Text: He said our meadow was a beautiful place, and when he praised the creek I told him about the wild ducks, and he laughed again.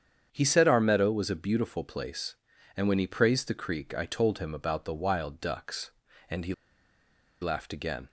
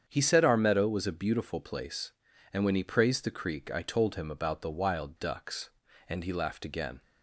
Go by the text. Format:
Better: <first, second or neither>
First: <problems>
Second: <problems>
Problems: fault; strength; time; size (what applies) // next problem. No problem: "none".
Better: second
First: starts louder than the rest; strong; until 1.3 s; 8 dB // pauses between "he" and "laughed"; noticeable; at 6.5 s; 0.87 s long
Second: starts louder than the rest; strong; until 1.0 s; 8 dB